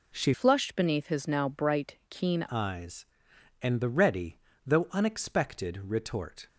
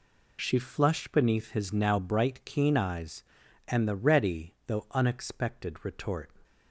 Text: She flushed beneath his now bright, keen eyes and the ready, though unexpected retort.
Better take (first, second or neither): second